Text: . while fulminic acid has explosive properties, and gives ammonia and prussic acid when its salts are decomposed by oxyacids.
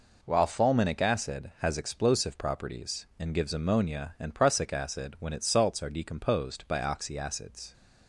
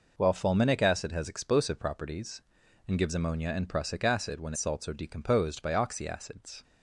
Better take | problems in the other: first | skips "its"; at 4.5 s

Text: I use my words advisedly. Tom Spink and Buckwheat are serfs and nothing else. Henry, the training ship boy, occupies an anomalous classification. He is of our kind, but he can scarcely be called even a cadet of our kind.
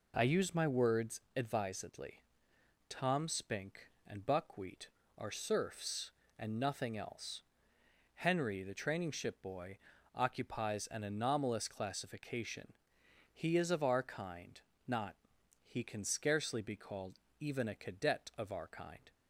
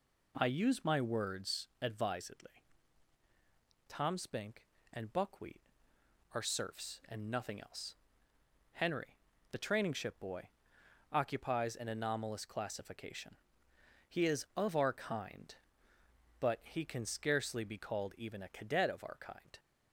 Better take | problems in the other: second | pauses between "words" and "advisedly"; slight; at 1.1 s; 0.16 s long // says "not" for "but"; at 14.8 s // pauses between "called" and "even"; slight; at 17.1 s; 0.22 s long

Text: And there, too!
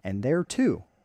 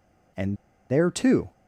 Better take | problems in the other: first | pauses between "And" and "there"; at 0.5 s; 0.36 s long

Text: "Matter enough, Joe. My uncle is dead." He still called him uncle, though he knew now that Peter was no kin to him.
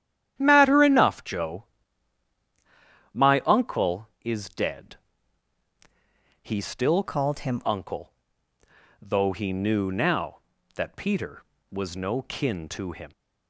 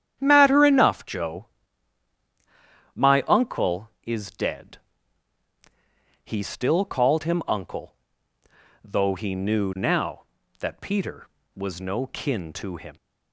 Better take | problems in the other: second | starts louder than the rest; strong; until 1.3 s; 10.5 dB; strong in the second // changes voice from "called" to "him"; from 7.0 to 7.6 s; 0.6 s long

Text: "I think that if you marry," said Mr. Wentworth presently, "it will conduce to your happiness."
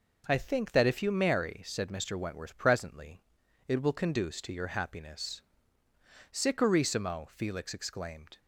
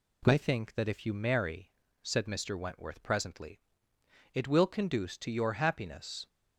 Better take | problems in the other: second | goes on to say "Sicurissimo Felix exclaimed"; strong; from 6.3 s on; 2.0 s long

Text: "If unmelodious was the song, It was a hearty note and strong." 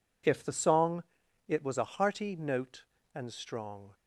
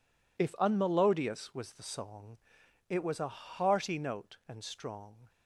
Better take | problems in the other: second | skips "unmelodious was"; at 0.4 s

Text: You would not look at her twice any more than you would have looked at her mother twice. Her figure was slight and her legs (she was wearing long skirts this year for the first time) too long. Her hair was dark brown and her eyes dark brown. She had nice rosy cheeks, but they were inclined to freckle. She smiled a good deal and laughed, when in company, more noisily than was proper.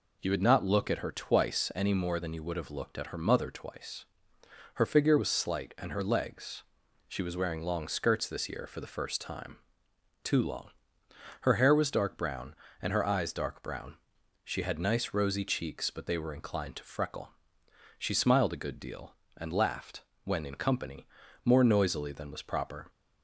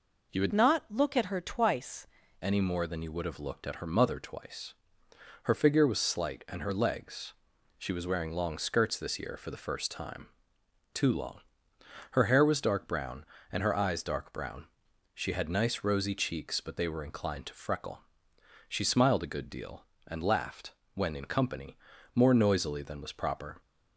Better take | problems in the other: first | changes voice from "not" to "twice"; from 0.5 to 2.0 s; 1.5 s long

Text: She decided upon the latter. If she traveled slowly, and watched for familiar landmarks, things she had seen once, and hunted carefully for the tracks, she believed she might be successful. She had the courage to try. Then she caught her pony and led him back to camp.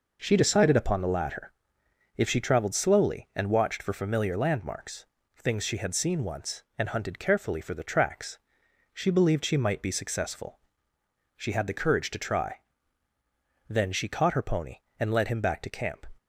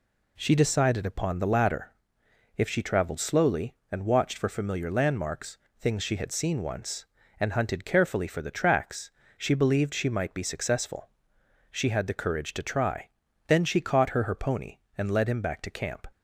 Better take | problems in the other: first | says "her" twice; at 14.2 s

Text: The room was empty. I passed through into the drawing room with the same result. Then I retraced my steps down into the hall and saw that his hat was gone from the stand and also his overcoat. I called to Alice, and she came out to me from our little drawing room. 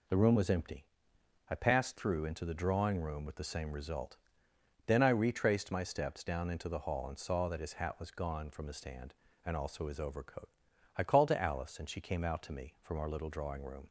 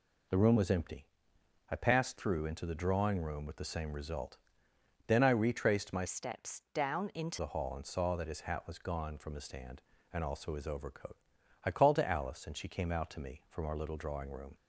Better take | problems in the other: first | changes voice from "steps" to "into"; from 6.0 to 7.3 s; 1.3 s long

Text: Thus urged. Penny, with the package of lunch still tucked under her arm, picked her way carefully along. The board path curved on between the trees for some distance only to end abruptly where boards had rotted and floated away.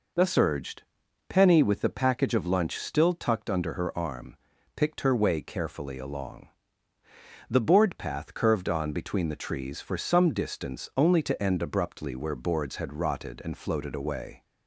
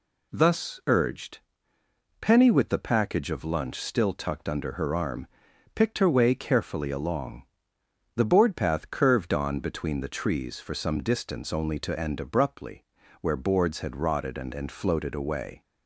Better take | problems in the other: first | pauses between "abruptly" and "where"; slight; at 12.8 s; 0.36 s long // says "and" twice; at 14.5 s

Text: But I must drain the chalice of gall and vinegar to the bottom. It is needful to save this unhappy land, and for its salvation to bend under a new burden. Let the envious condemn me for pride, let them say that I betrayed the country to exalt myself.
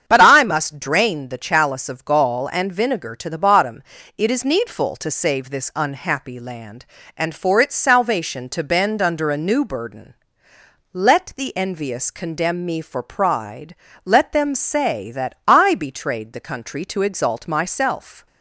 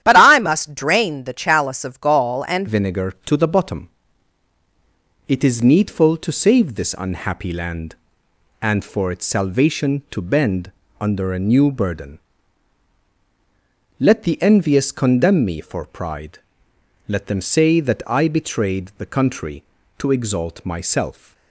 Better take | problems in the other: first | starts louder than the rest; strong; until 1.0 s; 11 dB; strong in the first // changes voice at "vinegar"; from 2.6 s on; 18.7 s long // pauses between "bend" and "under"; slight; at 10.7 s; 0.28 s long

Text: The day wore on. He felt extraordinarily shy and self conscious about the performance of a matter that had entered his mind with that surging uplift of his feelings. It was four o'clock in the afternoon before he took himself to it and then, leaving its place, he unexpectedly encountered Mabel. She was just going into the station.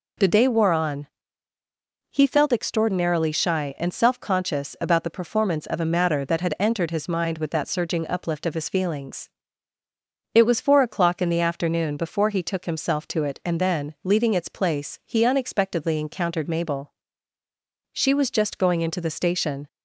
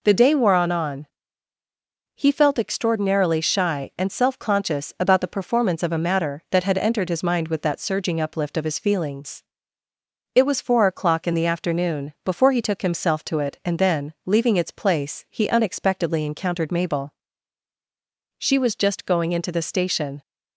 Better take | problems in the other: first | says "on" twice; at 0.7 s

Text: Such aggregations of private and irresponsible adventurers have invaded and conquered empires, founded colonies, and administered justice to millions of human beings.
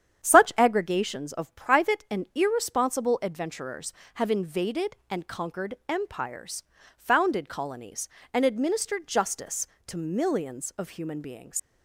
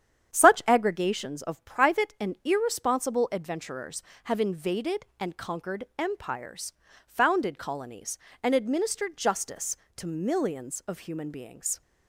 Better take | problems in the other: second | starts louder than the rest; strong; until 1.2 s; 9 dB; strong in the second // pauses between "conquered" and "empires"; slight; at 5.7 s; 0.16 s long; slight in the second // leaves "beings" unfinished; at 11.5 s; 120 ms

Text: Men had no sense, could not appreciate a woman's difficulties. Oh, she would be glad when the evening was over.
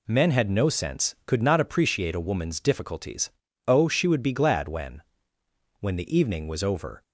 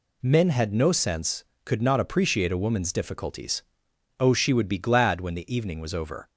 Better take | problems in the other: second | says "when" twice; at 5.8 s

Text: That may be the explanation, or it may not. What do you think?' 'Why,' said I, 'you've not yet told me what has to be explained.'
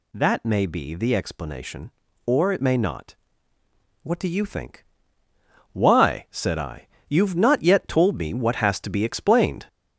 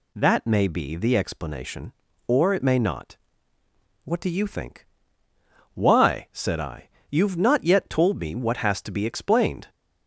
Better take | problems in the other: second | gets louder; noticeable; throughout; 4.5 dB

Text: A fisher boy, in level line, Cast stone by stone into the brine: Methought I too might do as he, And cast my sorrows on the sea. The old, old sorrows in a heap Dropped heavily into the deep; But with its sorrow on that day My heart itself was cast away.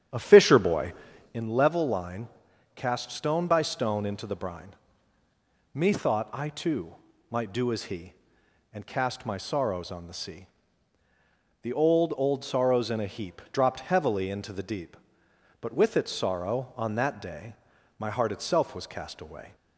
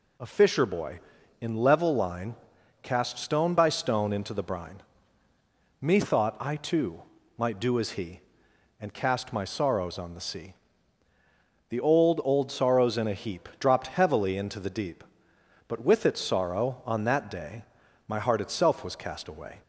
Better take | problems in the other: second | starts louder than the rest; strong; until 1.4 s; 9 dB // pauses between "too" and "might"; slight; at 6.9 s; 0.36 s long; slight in the second // pauses between "day" and "My"; at 17.5 s; 0.42 s long; also in the second

